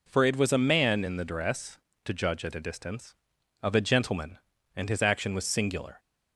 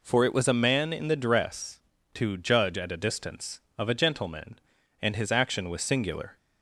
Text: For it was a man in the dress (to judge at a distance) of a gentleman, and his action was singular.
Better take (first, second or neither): neither